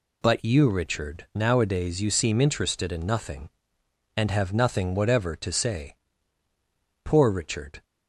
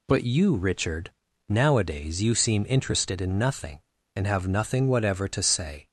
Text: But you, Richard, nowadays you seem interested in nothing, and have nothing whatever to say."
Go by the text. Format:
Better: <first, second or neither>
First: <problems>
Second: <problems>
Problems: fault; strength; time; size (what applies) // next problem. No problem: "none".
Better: second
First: goes on to say "Poor Richard"; noticeable; from 7.0 s on; 0.80 s long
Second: none